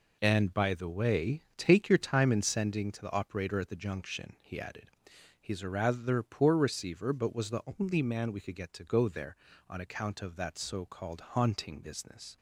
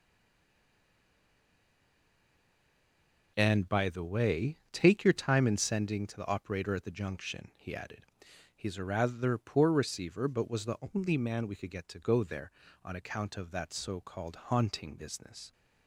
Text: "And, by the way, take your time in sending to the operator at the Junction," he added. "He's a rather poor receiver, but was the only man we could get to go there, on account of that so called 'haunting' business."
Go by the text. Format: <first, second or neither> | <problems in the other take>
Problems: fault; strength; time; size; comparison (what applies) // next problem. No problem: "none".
first | stays silent before the first word; strong; until 3.3 s; 3.3 s long // pauses between "the" and "only"; slight; at 10.7 s; 0.16 s long; slight in the first